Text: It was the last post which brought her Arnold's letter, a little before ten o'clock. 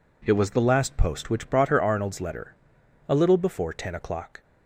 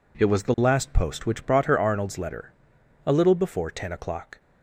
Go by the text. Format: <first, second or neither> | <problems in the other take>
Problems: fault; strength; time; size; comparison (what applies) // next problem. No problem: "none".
neither | none